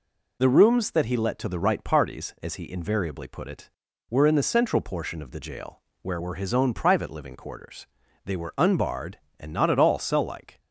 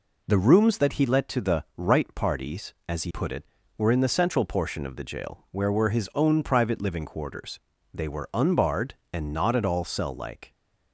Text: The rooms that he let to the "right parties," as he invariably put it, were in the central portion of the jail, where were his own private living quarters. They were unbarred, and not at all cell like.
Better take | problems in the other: first | skips "invariably"; at 3.1 s

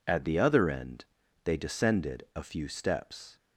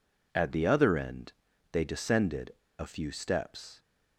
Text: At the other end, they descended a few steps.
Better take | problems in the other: first | pauses between "descended" and "a"; slight; at 2.5 s; 0.26 s long

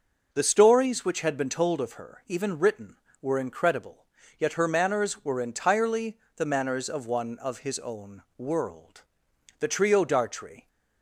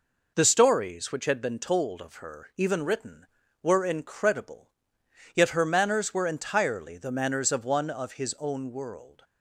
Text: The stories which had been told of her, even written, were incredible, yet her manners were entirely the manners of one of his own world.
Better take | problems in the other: second | pauses between "entirely" and "the"; slight; at 6.1 s; 0.22 s long // pauses between "own" and "world"; slight; at 8.2 s; 0.18 s long // goes on to say "The trio Dartrey"; noticeable; from 9.5 s on; 1.0 s long

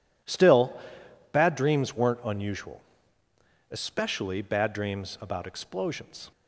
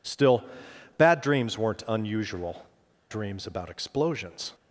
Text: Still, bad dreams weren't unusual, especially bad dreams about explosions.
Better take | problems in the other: first | skips "especially bad"; at 2.8 s

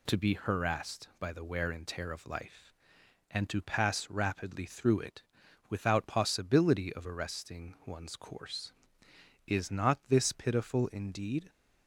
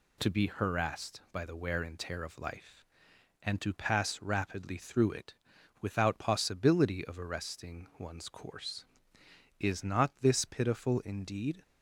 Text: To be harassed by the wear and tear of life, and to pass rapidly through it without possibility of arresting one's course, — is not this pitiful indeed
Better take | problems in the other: neither | pauses between "it" and "without"; noticeable; the same in both

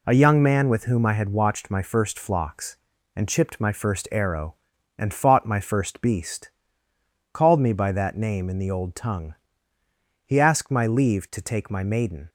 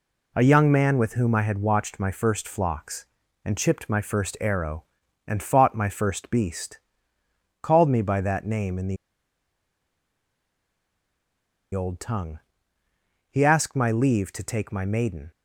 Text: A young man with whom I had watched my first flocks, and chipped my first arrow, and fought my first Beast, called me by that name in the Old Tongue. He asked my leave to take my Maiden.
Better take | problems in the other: first | pauses between "the" and "Old"; strong; at 8.9 s; 2.7 s long

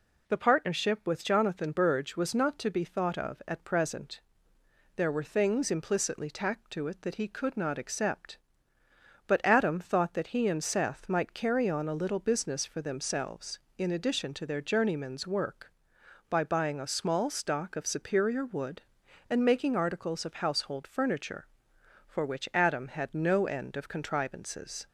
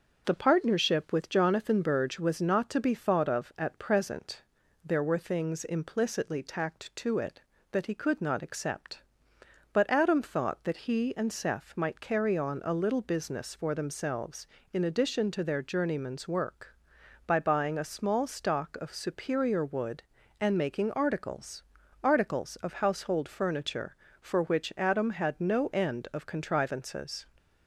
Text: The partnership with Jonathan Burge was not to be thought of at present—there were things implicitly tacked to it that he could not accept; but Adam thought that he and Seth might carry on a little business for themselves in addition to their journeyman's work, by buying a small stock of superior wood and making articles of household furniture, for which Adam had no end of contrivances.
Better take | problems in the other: first | starts louder than the rest; noticeable; until 1.2 s; 6 dB // says "articles" twice; at 22.0 s

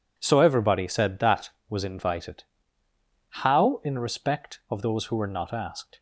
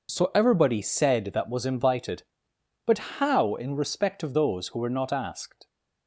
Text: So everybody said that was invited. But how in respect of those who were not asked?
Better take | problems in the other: second | skips "But"; at 2.9 s

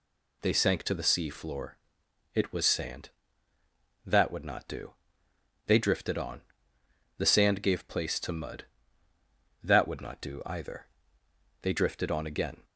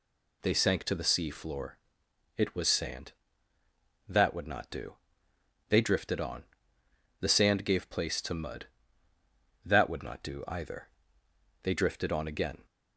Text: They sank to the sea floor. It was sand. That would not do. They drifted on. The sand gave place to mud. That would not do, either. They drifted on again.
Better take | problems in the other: neither | none

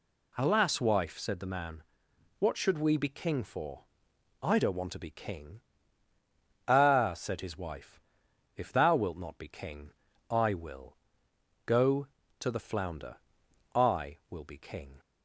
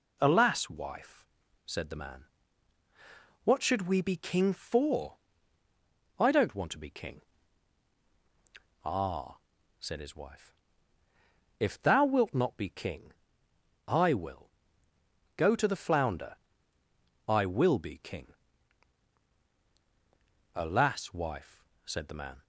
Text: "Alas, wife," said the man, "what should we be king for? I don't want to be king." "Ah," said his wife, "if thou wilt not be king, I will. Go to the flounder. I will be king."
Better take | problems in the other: first | goes on to say "Alas wife said the man"; strong; from 20.5 s on; 1.8 s long

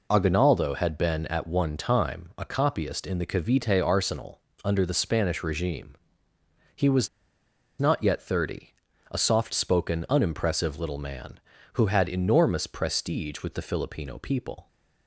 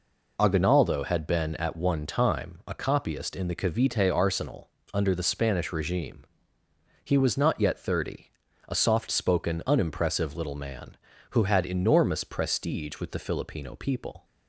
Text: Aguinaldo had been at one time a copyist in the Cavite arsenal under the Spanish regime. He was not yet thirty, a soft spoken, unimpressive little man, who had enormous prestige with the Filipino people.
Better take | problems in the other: second | pauses between "arsenal" and "under"; slight; at 4.3 s; 0.24 s long; slight in the second // pauses between "was" and "not"; noticeable; at 7.0 s; 0.71 s long

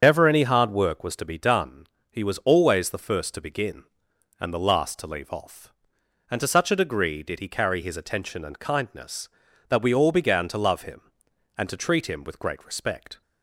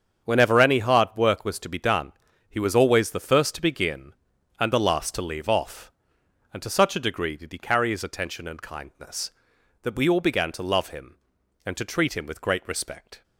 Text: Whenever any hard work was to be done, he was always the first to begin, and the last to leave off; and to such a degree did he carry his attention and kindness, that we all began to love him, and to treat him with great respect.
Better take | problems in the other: second | loses the start of "Whenever"; at 0.0 s; 160 ms // starts louder than the rest; strong; until 1.0 s; 7.5 dB; strong in the second

